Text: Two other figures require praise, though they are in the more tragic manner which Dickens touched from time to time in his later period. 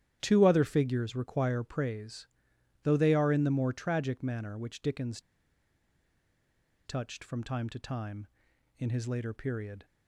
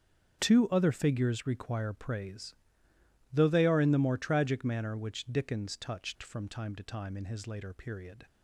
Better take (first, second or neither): second